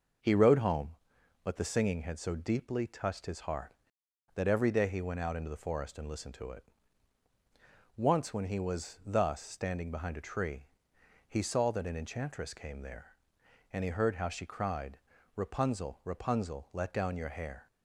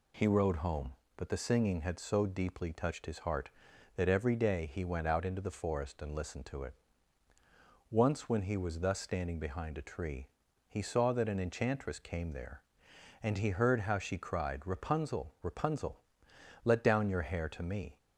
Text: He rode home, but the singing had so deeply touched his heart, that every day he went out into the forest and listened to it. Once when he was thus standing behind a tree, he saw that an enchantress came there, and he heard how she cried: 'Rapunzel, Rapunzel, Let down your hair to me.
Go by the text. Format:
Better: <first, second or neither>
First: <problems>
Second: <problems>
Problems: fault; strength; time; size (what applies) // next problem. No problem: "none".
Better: second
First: stops before "to me"; at 17.6 s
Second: none